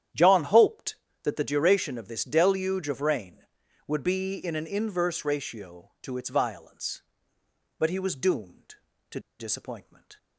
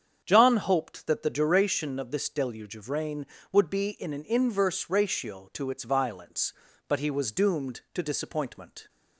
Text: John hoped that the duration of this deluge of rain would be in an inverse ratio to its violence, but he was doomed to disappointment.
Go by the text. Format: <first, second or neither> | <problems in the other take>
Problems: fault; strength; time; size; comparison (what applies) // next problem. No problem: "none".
second | starts louder than the rest; strong; until 1.4 s; 10 dB; strong in the second // pauses between "to" and "disappointment"; slight; at 9.1 s; 0.19 s long